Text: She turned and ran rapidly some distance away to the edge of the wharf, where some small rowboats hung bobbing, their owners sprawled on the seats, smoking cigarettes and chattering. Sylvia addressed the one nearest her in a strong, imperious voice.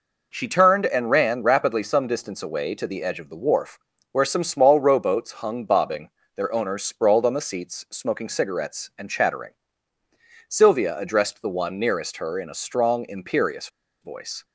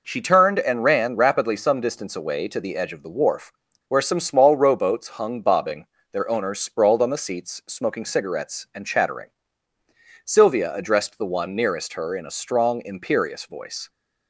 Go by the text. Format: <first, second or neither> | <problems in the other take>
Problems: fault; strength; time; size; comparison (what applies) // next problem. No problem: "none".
second | pauses between "imperious" and "voice"; slight; at 13.6 s; 0.34 s long